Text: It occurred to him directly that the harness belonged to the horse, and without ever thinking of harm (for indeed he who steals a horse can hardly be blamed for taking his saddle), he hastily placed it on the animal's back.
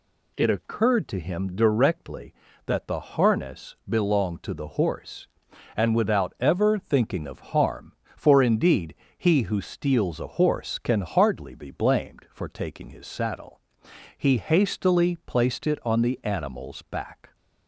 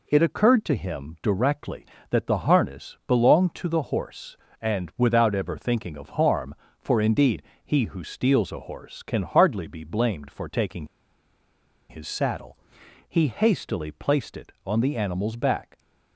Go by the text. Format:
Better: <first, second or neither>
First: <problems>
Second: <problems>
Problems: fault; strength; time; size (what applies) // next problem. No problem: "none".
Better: first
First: pauses between "indeed" and "he"; slight; at 8.9 s; 0.20 s long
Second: pauses between "indeed" and "he"; slight; at 7.4 s; 0.22 s long // pauses between "taking" and "his"; at 10.8 s; 1.0 s long